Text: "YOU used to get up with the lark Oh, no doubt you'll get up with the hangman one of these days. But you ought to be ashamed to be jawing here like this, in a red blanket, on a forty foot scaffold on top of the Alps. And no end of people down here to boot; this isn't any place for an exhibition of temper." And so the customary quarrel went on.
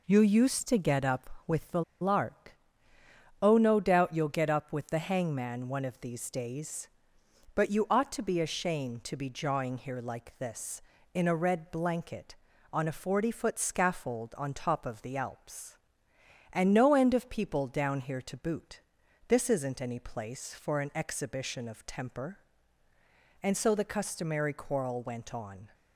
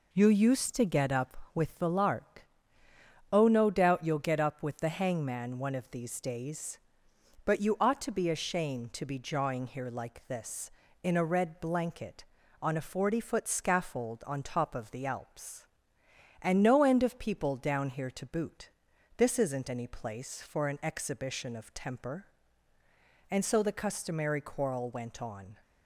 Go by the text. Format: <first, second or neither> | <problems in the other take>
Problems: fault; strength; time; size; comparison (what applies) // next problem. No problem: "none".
second | pauses between "the" and "lark"; slight; at 1.8 s; 0.19 s long // pauses between "lark" and "Oh"; noticeable; at 2.5 s; 0.88 s long; noticeable in the second